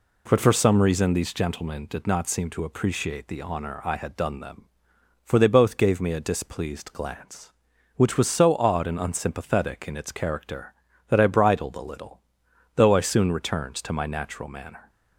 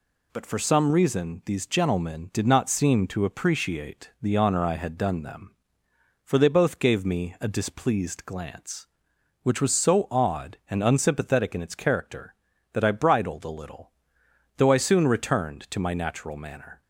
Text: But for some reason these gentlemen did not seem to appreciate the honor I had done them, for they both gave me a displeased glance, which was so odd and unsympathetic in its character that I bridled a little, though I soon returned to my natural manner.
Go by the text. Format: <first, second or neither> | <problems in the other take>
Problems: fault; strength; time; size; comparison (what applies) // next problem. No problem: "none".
neither | none